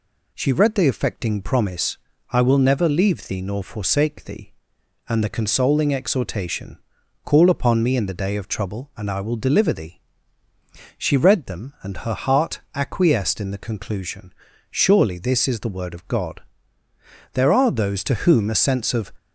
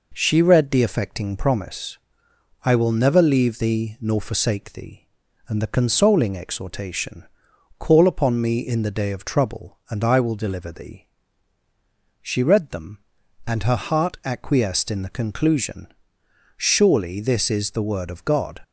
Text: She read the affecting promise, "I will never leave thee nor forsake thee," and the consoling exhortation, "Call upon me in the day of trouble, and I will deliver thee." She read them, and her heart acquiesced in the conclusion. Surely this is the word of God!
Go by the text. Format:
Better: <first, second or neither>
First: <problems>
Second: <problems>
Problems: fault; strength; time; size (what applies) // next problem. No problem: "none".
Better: second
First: goes on to say "There are those to whom a sense of"; strong; from 17.3 s on; 1.7 s long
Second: none